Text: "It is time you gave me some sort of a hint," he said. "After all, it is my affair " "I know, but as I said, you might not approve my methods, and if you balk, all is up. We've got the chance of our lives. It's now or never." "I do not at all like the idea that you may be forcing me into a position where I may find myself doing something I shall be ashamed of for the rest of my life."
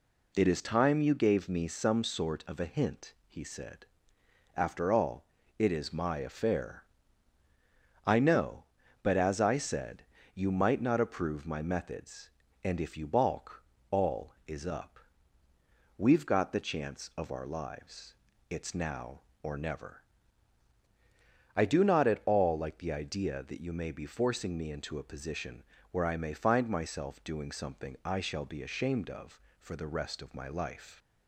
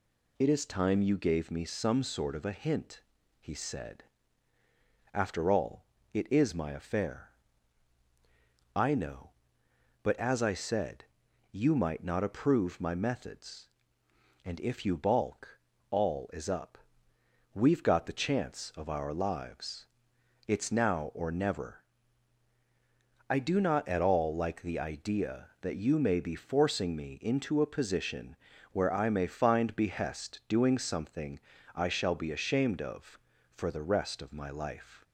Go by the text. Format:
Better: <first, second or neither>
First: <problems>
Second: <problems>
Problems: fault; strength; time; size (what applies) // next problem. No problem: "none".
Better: first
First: pauses between "position" and "where"; slight; at 25.6 s; 0.28 s long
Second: pauses between "position" and "where"; slight; at 28.3 s; 0.36 s long // says "behest" for "myself"; at 29.7 s // pauses between "something" and "I"; slight; at 31.3 s; 0.34 s long